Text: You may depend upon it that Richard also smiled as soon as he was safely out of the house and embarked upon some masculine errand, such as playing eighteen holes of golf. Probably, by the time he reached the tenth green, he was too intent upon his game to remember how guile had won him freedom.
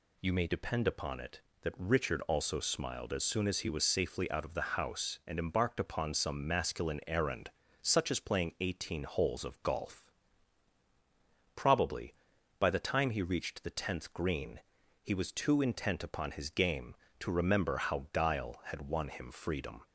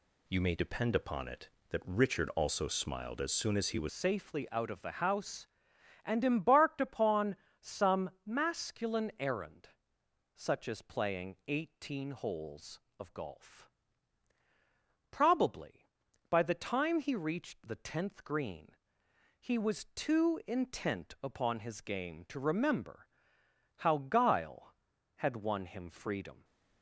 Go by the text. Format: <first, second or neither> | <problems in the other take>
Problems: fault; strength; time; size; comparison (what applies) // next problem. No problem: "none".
first | changes voice at "safely"; from 3.8 s on; 22.6 s long // pauses between "upon" and "some"; slight; at 7.3 s; 0.24 s long // pauses between "some" and "masculine"; slight; at 8.0 s; 0.16 s long // pauses between "remember" and "how"; noticeable; at 23.0 s; 0.70 s long